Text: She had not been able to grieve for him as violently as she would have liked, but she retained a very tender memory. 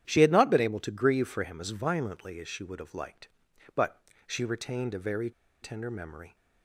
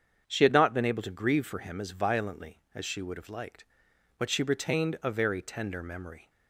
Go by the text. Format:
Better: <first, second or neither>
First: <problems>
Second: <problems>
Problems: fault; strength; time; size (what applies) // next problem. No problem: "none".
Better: second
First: starts louder than the rest; strong; until 1.1 s; 10.5 dB // pauses between "but" and "she"; slight; at 3.9 s; 0.28 s long // pauses between "very" and "tender"; slight; at 5.2 s; 0.32 s long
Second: starts louder than the rest; strong; until 1.2 s; 7.5 dB